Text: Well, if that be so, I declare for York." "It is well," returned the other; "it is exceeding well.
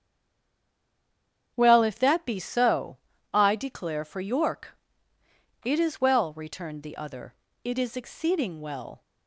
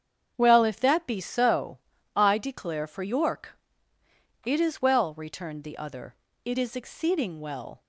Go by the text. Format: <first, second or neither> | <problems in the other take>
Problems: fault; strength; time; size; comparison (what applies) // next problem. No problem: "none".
second | stays silent before the first word; noticeable; until 1.5 s; 1.5 s long // starts louder than the rest; strong; until 2.5 s; 8 dB; strong in the second